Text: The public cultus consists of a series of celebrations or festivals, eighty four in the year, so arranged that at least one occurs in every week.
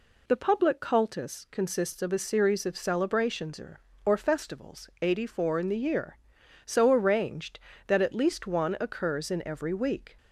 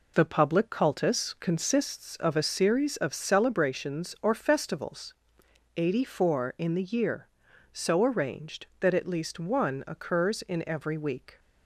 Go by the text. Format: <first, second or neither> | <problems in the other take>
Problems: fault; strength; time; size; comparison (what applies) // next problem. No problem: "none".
second | says "or" twice; at 4.0 s